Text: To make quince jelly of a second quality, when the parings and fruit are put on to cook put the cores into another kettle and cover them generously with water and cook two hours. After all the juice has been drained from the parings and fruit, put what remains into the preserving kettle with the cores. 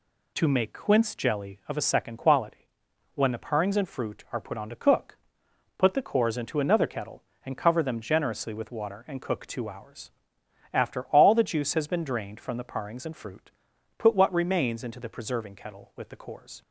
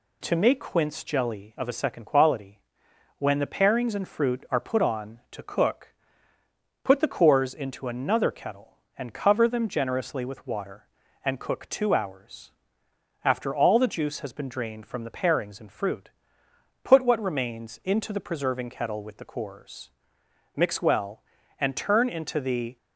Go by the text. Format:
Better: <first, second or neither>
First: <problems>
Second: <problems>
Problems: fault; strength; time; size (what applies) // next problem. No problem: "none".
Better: first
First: pauses between "cook" and "put"; noticeable; at 5.1 s; 0.60 s long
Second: pauses between "cook" and "put"; noticeable; at 5.9 s; 0.90 s long // goes on to say "Mix well and turn into the"; strong; from 20.5 s on; 2.2 s long